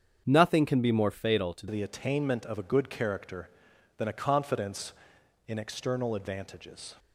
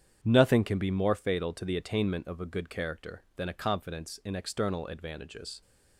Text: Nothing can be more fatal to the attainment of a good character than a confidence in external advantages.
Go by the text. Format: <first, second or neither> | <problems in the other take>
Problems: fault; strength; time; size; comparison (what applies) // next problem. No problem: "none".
second | starts louder than the rest; strong; until 1.2 s; 7.5 dB; strong in the second // changes voice at "the"; from 1.7 s on; 5.2 s long